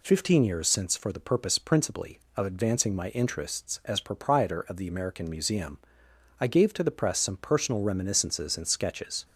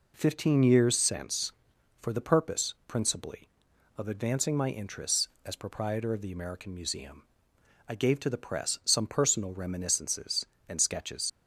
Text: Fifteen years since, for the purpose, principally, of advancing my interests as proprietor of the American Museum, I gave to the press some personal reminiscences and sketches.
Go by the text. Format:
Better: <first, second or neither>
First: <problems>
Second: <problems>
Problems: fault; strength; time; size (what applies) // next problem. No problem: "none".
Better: first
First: none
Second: leaves "sketches" unfinished; at 11.2 s; 50 ms